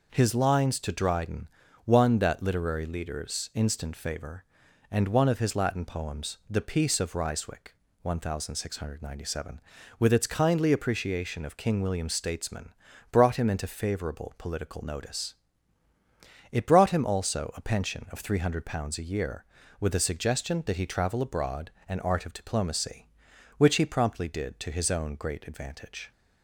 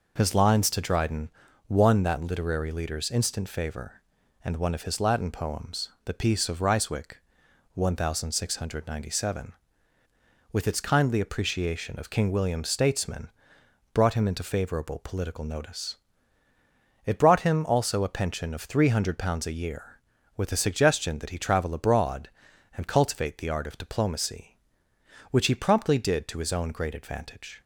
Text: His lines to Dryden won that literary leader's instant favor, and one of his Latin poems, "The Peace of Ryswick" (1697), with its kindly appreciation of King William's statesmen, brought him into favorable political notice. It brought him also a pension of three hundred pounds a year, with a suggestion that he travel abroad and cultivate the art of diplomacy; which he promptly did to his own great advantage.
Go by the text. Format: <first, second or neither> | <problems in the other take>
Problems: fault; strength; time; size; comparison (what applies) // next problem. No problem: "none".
second | pauses between "Dryden" and "won"; at 1.4 s; 0.38 s long; also in the second // skips "cultivate the"; at 22.0 s